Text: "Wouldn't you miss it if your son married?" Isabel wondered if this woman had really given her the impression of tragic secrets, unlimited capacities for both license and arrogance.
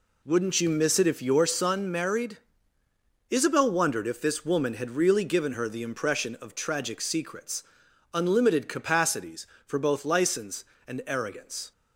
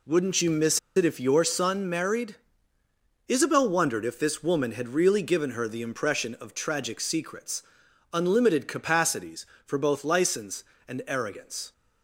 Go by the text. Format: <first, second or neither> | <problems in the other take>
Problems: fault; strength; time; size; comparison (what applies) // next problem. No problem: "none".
first | pauses between "miss" and "it"; slight; at 0.7 s; 0.18 s long